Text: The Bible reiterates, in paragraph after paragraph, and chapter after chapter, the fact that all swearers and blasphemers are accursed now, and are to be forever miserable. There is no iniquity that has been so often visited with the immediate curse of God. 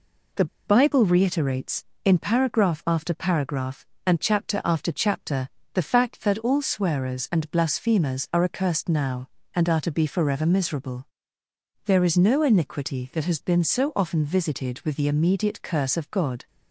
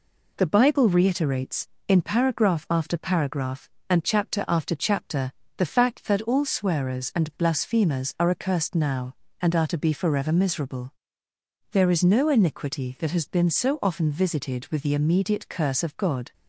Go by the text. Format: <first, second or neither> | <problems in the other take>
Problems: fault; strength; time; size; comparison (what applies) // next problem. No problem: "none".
second | pauses between "The" and "Bible"; slight; at 0.4 s; 0.22 s long